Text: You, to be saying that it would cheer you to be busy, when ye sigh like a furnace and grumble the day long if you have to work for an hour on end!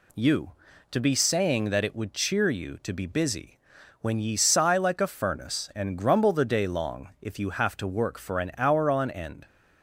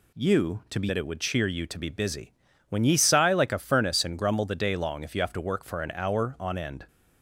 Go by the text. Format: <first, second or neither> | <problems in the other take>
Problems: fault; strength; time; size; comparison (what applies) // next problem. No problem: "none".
first | skips "saying"; at 0.8 s